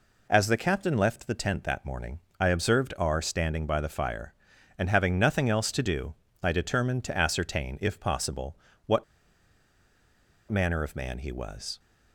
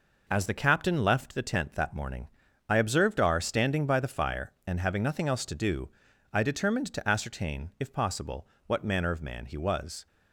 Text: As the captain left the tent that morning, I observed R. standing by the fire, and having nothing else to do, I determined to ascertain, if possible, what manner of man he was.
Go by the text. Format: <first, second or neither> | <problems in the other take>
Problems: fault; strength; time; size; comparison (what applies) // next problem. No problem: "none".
second | pauses between "what" and "manner"; strong; at 9.0 s; 1.4 s long